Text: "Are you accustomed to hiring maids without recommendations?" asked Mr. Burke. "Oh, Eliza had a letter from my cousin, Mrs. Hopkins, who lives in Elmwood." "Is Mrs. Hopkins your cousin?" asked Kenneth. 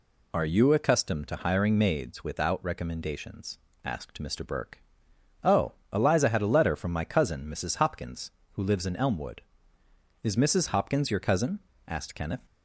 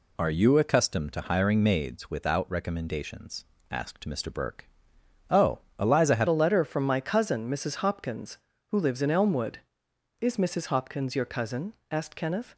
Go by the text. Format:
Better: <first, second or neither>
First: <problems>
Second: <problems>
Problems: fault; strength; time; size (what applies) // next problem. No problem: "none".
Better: first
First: none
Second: changes voice at "a"; from 6.2 s on; 6.3 s long